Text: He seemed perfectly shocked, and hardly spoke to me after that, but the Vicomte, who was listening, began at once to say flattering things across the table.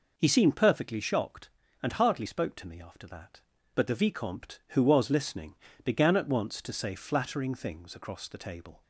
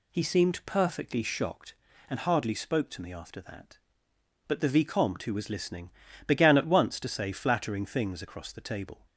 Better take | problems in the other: neither | none

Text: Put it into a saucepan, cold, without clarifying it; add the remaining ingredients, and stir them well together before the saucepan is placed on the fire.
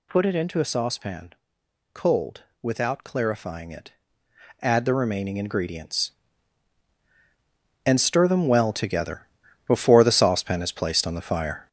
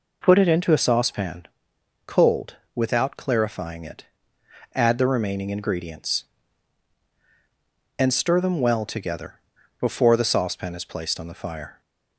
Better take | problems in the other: second | gets louder; noticeable; throughout; 6 dB // pauses between "together" and "before"; at 9.2 s; 0.40 s long; also in the second

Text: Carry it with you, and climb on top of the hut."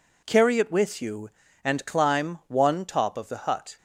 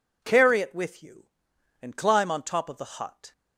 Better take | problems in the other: second | says "one" for "on"; at 2.4 s

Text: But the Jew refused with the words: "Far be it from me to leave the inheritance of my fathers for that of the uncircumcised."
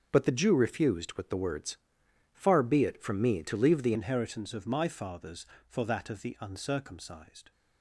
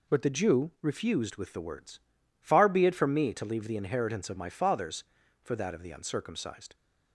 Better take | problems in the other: second | starts louder than the rest; until 1.1 s; 7 dB // changes voice at "inheritance"; from 3.9 s on; 3.6 s long

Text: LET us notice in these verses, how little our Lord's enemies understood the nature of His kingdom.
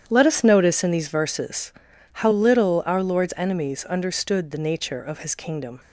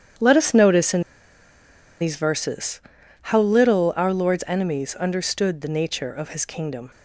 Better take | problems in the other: first | starts louder than the rest; strong; until 2.1 s; 9.5 dB; strong in the first // pauses between "in" and "these"; at 1.0 s; 0.98 s long

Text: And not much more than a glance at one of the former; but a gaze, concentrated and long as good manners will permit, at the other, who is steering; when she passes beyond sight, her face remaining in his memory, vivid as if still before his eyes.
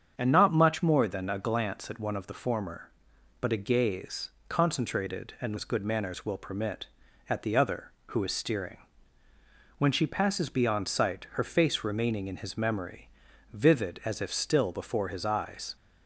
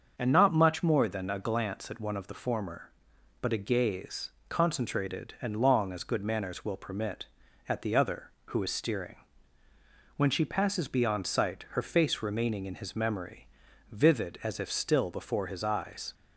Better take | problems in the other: second | starts louder than the rest; strong; until 1.1 s; 7.5 dB; also in the second // skips "long"; at 5.5 s

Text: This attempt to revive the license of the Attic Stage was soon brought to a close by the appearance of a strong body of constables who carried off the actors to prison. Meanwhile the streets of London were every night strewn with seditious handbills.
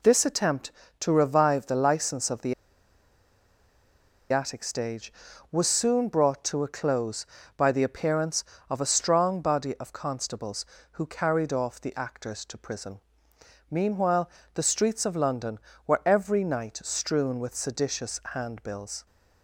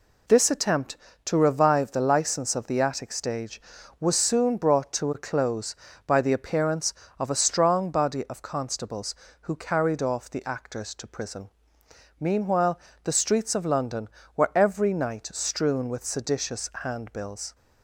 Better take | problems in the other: second | pauses between "the" and "Attic"; strong; at 2.5 s; 1.7 s long // pauses between "Meanwhile" and "the"; slight; at 14.2 s; 0.28 s long; slight in the second

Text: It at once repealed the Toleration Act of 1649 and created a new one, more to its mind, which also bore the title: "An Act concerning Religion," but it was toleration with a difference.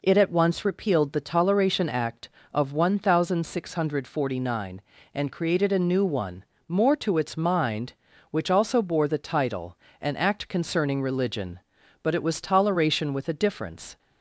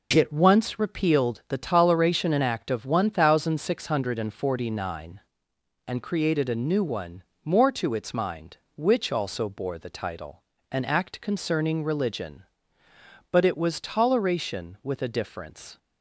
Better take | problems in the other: first | skips "at"; at 0.2 s

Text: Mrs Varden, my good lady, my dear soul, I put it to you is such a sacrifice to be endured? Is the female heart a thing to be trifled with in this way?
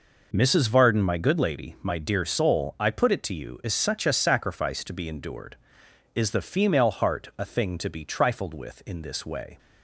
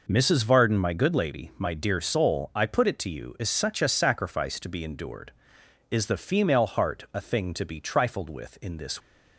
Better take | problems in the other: first | stops before "way"; at 9.0 s

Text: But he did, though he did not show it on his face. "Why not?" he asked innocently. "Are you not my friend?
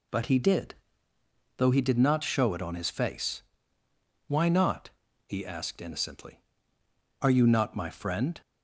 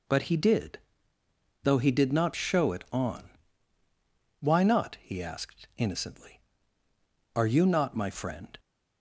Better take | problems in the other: first | skips "his face"; at 3.8 s

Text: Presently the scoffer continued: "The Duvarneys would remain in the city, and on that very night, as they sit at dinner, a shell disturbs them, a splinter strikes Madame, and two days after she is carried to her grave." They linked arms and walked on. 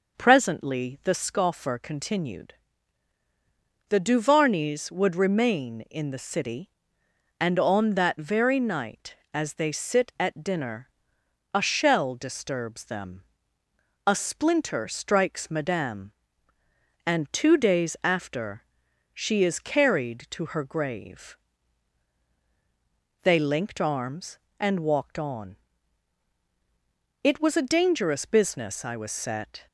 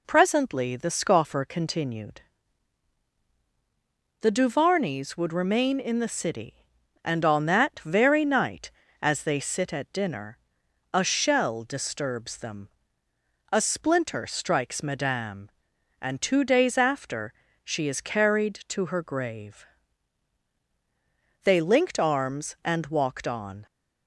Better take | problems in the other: second | pauses between "after" and "she"; noticeable; at 18.6 s; 0.50 s long; slight in the second // goes on to say "It was a dangerous business I was set"; strong; from 27.2 s on; 2.4 s long

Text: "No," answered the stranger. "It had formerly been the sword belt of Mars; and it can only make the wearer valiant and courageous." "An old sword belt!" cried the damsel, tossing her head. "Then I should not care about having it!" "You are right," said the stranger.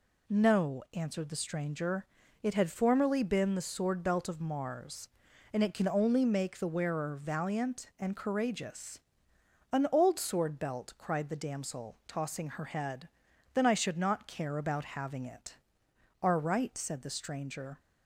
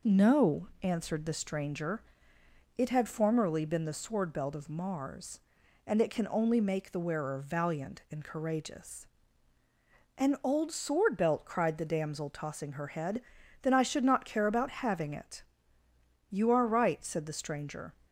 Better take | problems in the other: second | skips "You"; at 15.9 s

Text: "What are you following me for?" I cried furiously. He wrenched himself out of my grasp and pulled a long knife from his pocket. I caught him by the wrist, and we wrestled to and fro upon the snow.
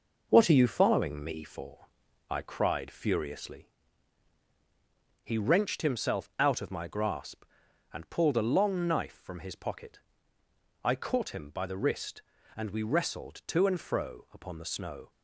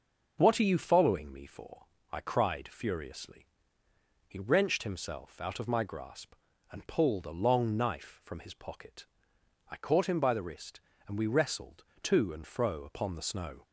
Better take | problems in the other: second | gets quieter; noticeable; throughout; 5 dB

